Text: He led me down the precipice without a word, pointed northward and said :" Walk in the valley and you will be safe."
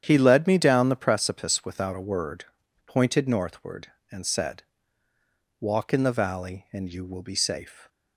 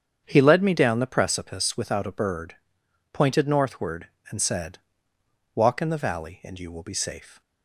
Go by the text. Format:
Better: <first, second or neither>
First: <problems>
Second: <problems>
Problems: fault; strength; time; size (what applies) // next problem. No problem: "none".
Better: first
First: starts louder than the rest; strong; until 1.0 s; 9.5 dB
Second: starts louder than the rest; strong; until 1.2 s; 8.5 dB // says "bird" for "word"; at 2.1 s